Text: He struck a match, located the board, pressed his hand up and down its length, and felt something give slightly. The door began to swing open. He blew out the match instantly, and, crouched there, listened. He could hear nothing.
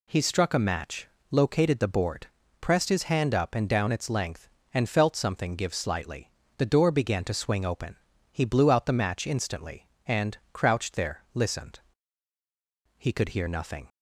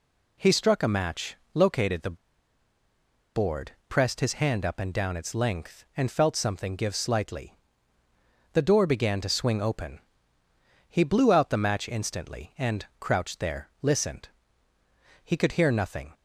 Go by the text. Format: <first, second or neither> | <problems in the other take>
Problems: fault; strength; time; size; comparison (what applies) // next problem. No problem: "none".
first | pauses between "the" and "board"; at 2.1 s; 1.1 s long